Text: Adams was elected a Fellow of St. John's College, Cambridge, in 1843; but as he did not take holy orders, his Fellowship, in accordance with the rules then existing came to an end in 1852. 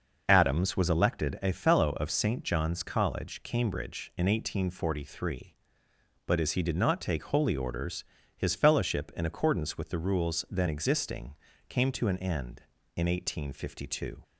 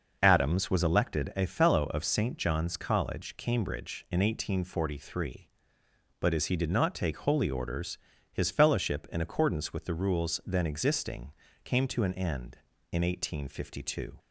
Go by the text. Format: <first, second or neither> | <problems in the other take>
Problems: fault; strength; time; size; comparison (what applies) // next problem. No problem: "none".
neither | pauses between "existing" and "came"; slight; the same in both